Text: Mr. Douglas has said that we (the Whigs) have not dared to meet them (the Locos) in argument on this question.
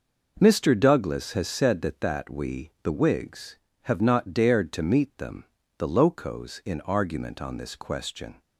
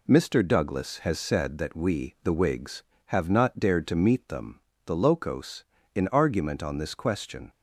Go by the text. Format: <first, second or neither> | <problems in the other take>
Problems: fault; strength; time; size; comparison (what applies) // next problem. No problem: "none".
second | says "that" twice; at 2.0 s